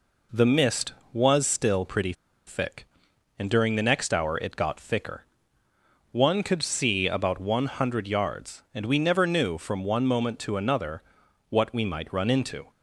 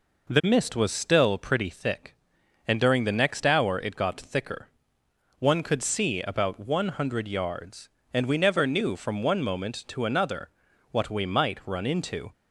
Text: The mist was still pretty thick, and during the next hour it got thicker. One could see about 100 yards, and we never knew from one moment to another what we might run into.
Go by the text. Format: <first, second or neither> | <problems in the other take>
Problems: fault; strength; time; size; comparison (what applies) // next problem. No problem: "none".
second | pauses between "pretty" and "thick"; slight; at 2.1 s; 0.33 s long // pauses between "another" and "what"; noticeable; at 11.0 s; 0.48 s long; also in the second